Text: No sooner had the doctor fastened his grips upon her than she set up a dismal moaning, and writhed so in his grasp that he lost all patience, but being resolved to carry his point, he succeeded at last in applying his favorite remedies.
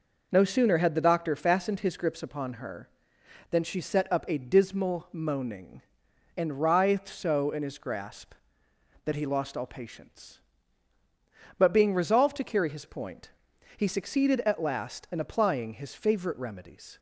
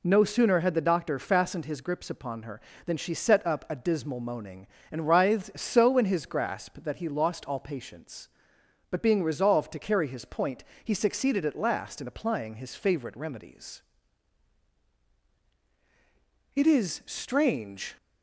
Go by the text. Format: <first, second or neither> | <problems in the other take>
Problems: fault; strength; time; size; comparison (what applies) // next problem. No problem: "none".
first | goes on to say "It is strange"; from 16.5 s on; 1.4 s long